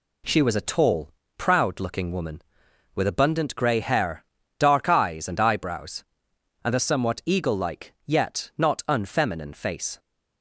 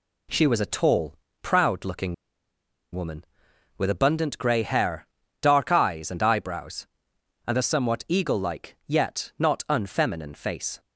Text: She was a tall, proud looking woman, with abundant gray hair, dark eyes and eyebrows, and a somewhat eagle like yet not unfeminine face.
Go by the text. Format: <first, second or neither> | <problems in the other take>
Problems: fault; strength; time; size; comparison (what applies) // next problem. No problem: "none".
first | pauses between "looking" and "woman"; noticeable; at 2.1 s; 0.78 s long